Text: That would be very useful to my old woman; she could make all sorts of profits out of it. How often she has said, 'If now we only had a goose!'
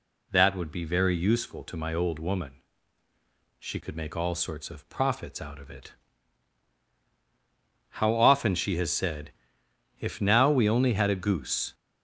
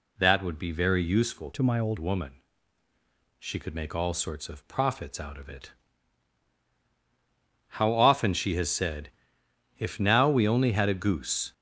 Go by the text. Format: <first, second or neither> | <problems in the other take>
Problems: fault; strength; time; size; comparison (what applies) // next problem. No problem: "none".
first | changes voice from "to" to "old"; from 1.5 to 1.9 s; 0.4 s long